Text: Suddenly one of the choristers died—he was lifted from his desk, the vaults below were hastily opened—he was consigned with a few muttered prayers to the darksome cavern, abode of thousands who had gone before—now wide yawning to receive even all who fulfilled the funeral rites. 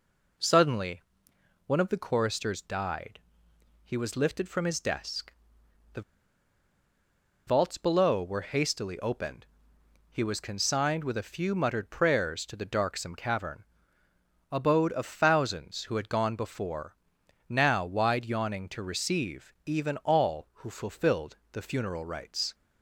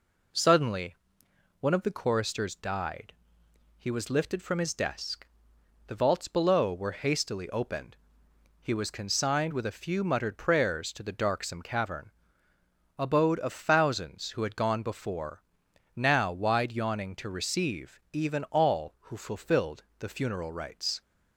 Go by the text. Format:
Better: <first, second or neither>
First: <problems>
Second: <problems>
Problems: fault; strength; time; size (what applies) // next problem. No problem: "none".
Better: second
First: pauses between "Suddenly" and "one"; noticeable; at 1.0 s; 0.66 s long // pauses between "the" and "vaults"; strong; at 6.0 s; 1.4 s long // pauses between "fulfilled" and "the"; slight; at 21.3 s; 0.16 s long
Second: pauses between "Suddenly" and "one"; noticeable; at 0.9 s; 0.66 s long // pauses between "fulfilled" and "the"; slight; at 19.8 s; 0.16 s long